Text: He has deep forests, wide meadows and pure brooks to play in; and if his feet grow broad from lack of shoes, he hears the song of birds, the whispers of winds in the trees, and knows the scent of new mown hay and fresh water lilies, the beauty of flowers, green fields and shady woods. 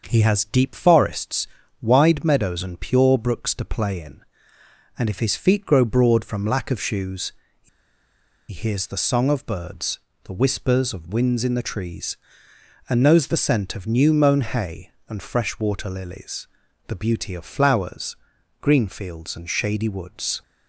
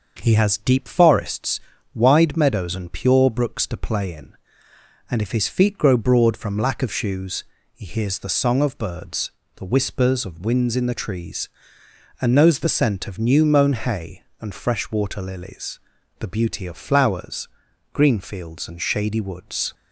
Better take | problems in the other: second | starts louder than the rest; until 1.0 s; 6 dB; also in the second // pauses between "he" and "hears"; noticeable; at 7.6 s; 0.82 s long

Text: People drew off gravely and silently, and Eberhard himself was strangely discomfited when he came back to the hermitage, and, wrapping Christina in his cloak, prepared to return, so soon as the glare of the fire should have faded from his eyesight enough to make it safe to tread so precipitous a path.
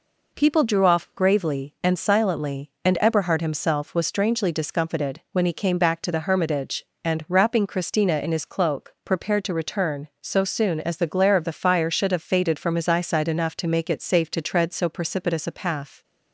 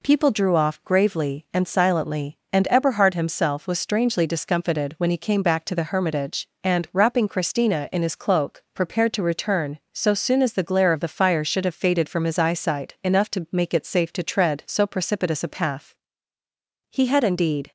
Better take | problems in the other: first | goes on to say "He had indeed"; noticeable; from 16.8 s on; 0.82 s long

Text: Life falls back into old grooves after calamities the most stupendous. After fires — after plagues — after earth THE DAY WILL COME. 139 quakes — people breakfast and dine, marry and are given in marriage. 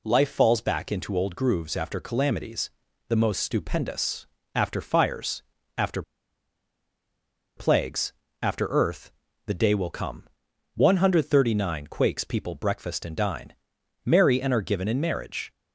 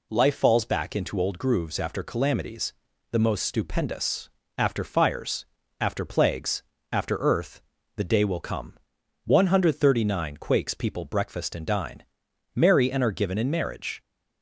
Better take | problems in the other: second | pauses between "calamities" and "the"; at 2.6 s; 0.38 s long; also in the second // pauses between "after" and "plagues"; strong; at 6.0 s; 1.5 s long // pauses between "earth" and "THE"; slight; at 9.1 s; 0.36 s long; slight in the second

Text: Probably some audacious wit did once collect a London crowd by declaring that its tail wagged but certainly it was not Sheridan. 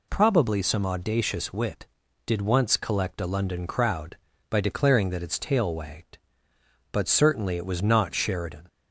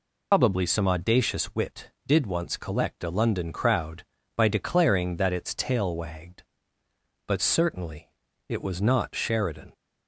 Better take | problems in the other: first | loses the start of "Probably"; at 0.3 s; 135 ms // pauses between "certainly" and "it"; at 8.0 s; 0.38 s long

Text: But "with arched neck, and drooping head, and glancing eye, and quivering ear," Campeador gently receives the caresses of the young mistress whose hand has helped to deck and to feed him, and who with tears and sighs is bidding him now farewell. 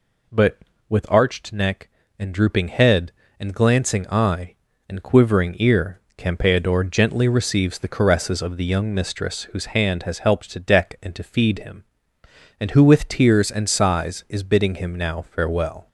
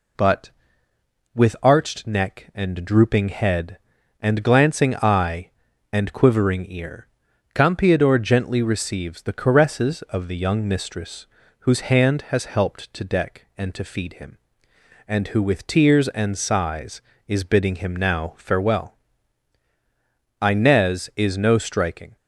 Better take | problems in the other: first | pauses between "mistress" and "whose"; slight; at 11.2 s; 0.34 s long // goes on to say "Inez is no striking"; strong; from 20.3 s on; 1.7 s long

